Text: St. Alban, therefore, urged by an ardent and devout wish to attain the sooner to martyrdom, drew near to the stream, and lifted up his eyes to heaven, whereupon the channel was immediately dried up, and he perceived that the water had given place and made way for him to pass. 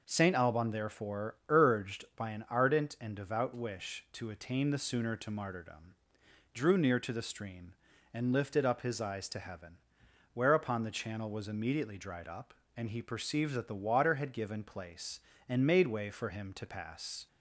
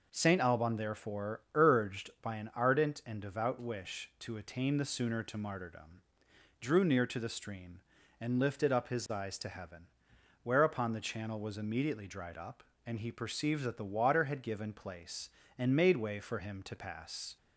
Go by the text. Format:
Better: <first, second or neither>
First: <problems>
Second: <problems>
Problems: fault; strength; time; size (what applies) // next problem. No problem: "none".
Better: neither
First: none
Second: none